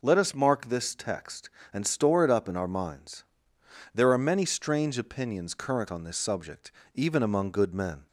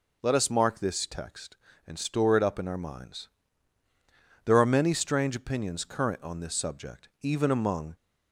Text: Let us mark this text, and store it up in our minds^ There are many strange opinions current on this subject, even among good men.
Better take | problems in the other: first | pauses between "minds" and "There"; at 3.2 s; 1.1 s long; noticeable in the first // stops before "good men"; at 7.9 s

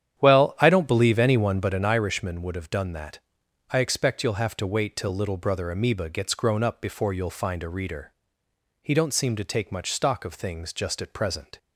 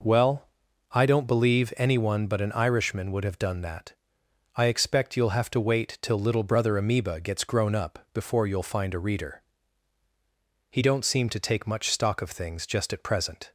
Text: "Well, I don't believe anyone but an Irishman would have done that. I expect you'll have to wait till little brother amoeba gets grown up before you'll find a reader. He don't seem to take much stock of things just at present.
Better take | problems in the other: second | starts louder than the rest; strong; until 2.0 s; 9.5 dB

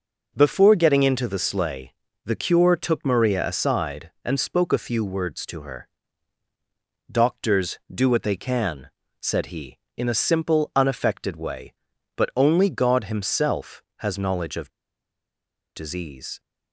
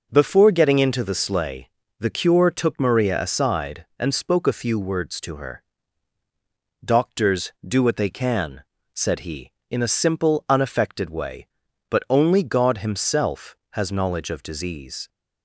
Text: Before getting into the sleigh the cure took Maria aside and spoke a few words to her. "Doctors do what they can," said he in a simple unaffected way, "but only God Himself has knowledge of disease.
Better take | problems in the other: second | pauses between "sleigh" and "the"; slight; at 1.9 s; 0.32 s long; slight in the second // pauses between "of" and "disease"; at 14.7 s; 1.0 s long

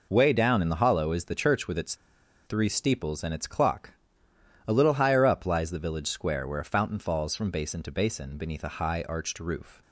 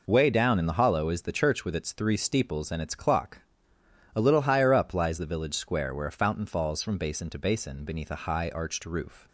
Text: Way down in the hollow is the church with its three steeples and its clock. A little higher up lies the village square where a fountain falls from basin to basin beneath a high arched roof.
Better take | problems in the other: second | pauses between "its" and "three"; noticeable; at 1.9 s; 0.51 s long

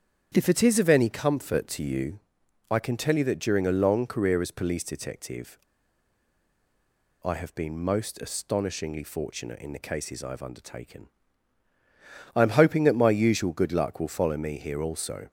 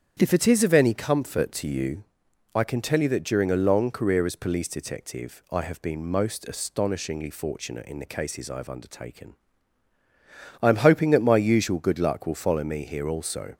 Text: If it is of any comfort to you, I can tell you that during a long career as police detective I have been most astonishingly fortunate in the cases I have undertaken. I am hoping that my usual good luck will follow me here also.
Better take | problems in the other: second | starts louder than the rest; strong; until 1.3 s; 8.5 dB; strong in the second // pauses between "detective" and "I"; strong; at 5.5 s; 1.6 s long

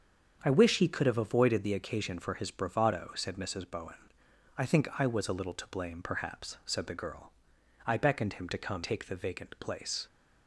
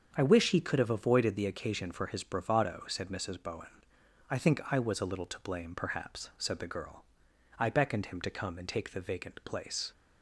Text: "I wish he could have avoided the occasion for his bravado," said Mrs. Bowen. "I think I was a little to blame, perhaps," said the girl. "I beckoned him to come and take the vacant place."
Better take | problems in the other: second | starts louder than the rest; strong; until 1.4 s; 7.5 dB; strong in the second // skips "and"; at 8.8 s

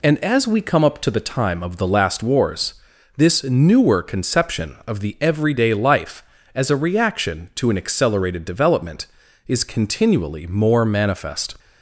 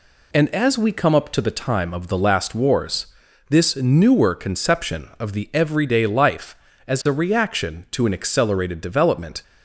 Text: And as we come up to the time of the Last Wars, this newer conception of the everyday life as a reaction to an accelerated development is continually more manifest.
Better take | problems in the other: first | stops before "is continually more manifest"; at 9.4 s

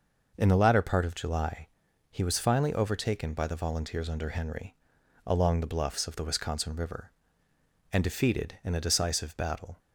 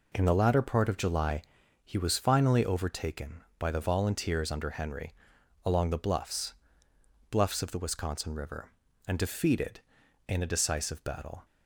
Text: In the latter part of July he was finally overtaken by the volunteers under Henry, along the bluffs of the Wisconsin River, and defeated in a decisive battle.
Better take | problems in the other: first | pauses between "July" and "he"; at 1.4 s; 0.44 s long; also in the first // says "bluffs" twice; at 7.3 s

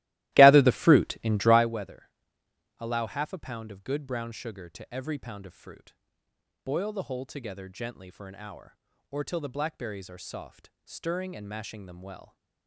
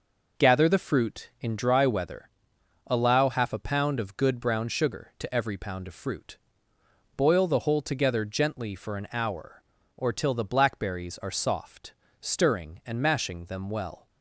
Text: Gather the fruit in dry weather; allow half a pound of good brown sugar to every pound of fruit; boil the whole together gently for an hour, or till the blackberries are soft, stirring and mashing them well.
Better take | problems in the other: second | starts louder than the rest; strong; until 1.7 s; 16.5 dB

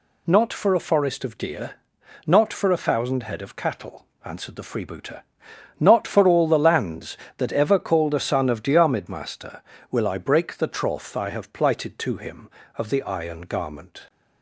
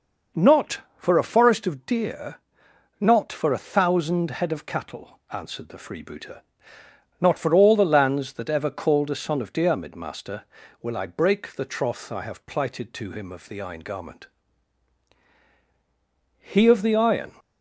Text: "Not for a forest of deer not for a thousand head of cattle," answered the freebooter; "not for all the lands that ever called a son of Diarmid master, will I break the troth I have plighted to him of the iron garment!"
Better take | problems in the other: first | pauses between "deer" and "not"; noticeable; at 2.3 s; 0.66 s long; noticeable in the first // goes on to say "He of the iron"; noticeable; from 16.3 s on; 0.94 s long

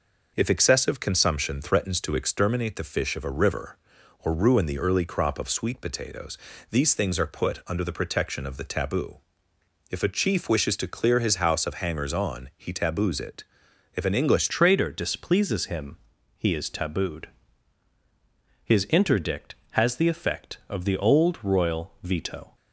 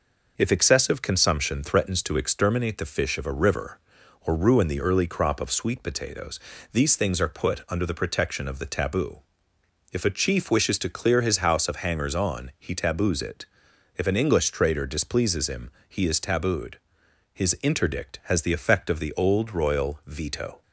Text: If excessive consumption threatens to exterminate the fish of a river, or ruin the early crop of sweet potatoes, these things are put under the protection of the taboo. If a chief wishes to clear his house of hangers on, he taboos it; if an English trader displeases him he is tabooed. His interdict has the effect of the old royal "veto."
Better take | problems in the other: second | changes voice at "trader"; from 14.4 s on; 8.1 s long // pauses between "him" and "he"; at 15.9 s; 0.40 s long; slight in the second

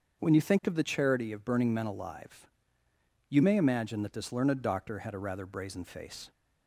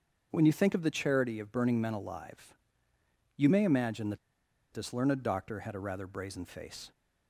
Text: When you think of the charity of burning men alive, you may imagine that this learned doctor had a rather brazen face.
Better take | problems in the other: first | starts louder than the rest; until 1.3 s; 7 dB; also in the first // pauses between "that" and "this"; noticeable; at 4.1 s; 0.56 s long

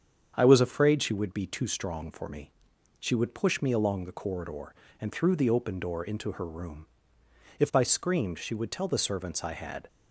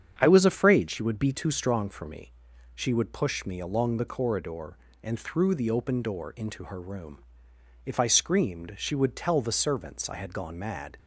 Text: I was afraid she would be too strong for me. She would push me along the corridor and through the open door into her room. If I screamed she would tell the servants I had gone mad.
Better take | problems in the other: second | starts louder than the rest; strong; until 1.3 s; 7.5 dB; strong in the second // stops before "gone mad"; at 9.8 s

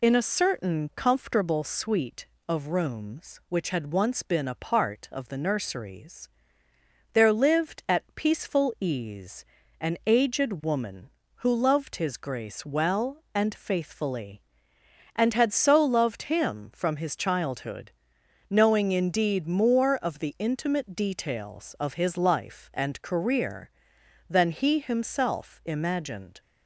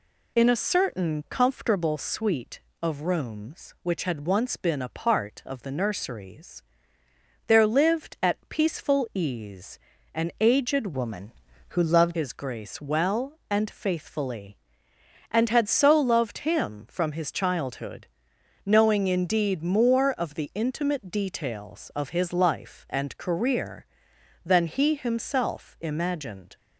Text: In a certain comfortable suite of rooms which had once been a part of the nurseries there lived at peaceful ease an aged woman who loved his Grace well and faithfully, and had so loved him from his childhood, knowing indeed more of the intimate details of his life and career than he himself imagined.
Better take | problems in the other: first | pauses between "nurseries" and "there"; noticeable; at 6.6 s; 0.86 s long; noticeable in the first // pauses between "ease" and "an"; slight; at 9.7 s; 0.36 s long; slight in the first // changes voice from "woman" to "loved"; from 10.9 to 12.1 s; 1.2 s long

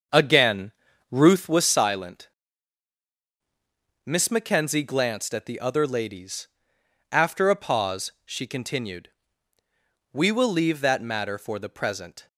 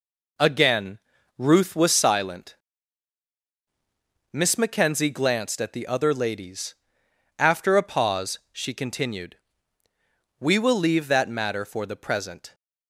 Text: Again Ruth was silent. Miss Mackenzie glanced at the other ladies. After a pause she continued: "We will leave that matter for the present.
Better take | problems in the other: second | starts louder than the rest; until 1.5 s; 6.5 dB // pauses between "Again" and "Ruth"; at 0.7 s; 0.40 s long; also in the second

